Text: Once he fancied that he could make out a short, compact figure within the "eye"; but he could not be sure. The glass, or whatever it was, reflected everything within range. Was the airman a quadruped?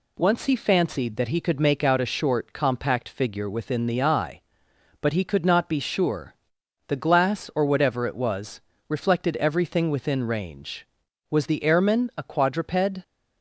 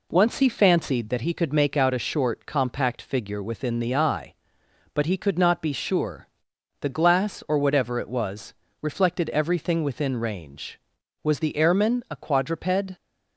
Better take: first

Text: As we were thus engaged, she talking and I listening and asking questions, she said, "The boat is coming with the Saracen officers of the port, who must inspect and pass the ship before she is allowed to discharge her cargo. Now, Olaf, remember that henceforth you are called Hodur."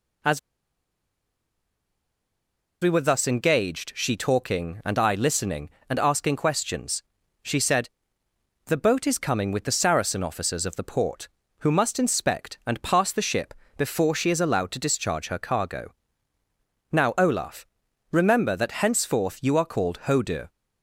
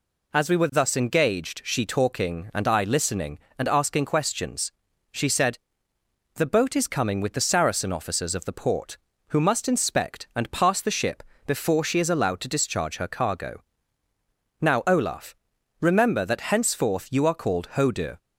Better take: second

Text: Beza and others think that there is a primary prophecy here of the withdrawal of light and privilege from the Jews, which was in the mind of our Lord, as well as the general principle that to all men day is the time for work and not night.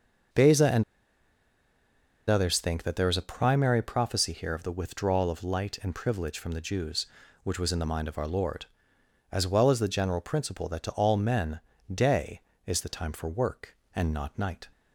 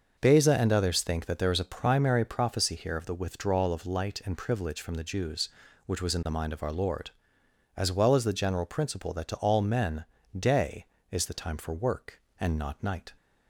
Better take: second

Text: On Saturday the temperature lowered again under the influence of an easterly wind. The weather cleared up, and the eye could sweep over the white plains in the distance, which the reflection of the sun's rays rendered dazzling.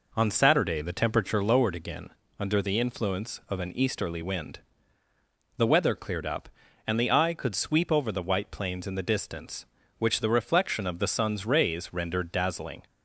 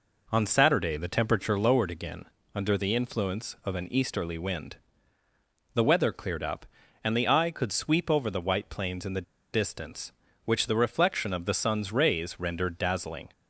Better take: first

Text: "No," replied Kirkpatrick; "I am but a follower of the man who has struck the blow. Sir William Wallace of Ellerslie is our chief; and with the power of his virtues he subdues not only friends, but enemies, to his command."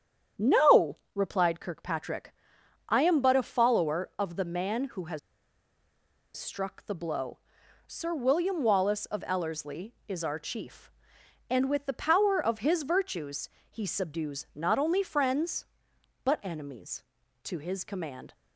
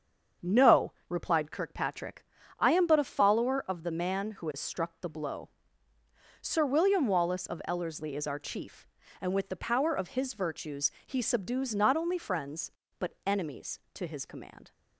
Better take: second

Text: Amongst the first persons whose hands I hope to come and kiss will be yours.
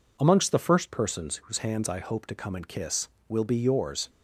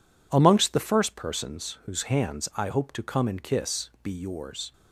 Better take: first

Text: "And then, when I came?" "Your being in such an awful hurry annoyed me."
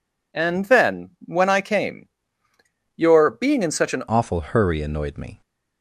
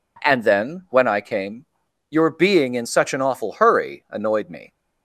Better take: second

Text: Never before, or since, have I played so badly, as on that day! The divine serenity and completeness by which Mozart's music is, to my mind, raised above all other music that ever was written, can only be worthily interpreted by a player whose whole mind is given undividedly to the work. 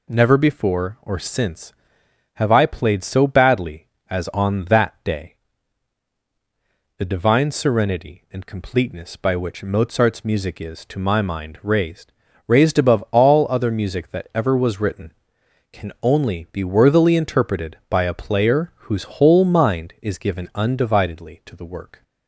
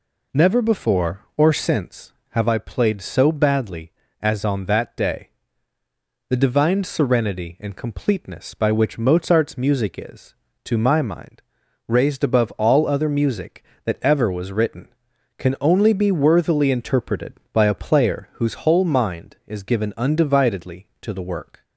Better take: second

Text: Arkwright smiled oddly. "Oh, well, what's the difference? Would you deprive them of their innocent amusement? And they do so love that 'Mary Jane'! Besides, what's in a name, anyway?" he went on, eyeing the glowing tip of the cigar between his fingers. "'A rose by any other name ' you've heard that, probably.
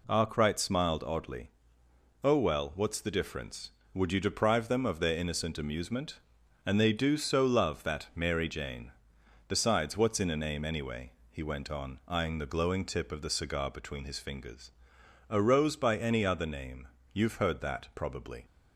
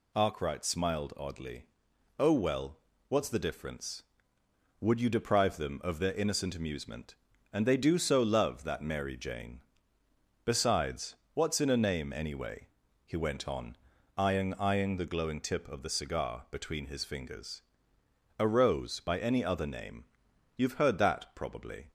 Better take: first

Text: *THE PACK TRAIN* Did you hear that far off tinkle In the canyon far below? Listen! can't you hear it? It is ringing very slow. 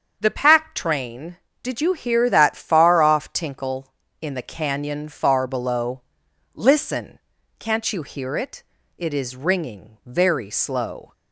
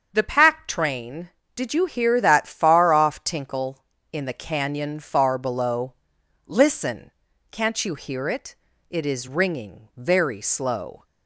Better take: neither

